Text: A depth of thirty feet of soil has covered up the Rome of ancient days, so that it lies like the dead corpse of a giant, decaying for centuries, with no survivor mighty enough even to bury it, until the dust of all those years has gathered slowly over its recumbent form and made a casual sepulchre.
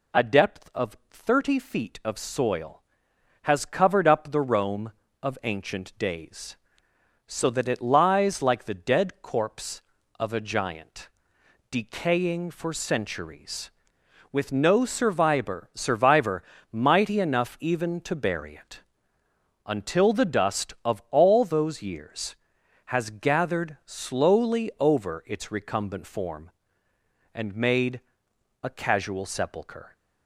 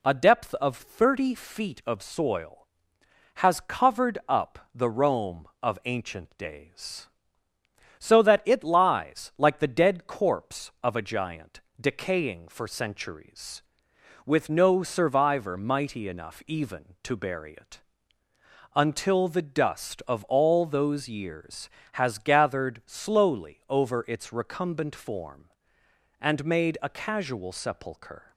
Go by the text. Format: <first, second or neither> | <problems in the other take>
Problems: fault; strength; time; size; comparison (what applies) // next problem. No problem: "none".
second | says "survivor" twice; at 15.7 s // pauses between "made" and "a"; noticeable; at 28.0 s; 0.62 s long